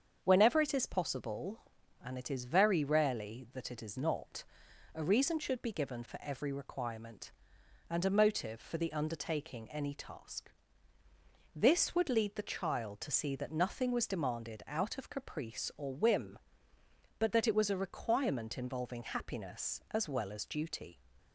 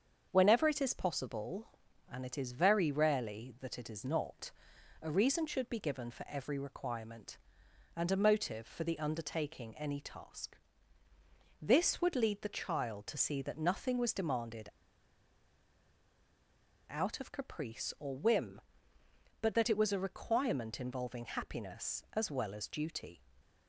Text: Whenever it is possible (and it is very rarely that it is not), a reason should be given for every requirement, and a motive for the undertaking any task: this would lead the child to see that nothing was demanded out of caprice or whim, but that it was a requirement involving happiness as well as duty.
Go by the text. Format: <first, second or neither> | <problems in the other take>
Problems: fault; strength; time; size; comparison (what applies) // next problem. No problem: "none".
first | starts louder than the rest; strong; until 1.3 s; 7.5 dB; strong in the first // pauses between "demanded" and "out"; strong; at 14.6 s; 2.1 s long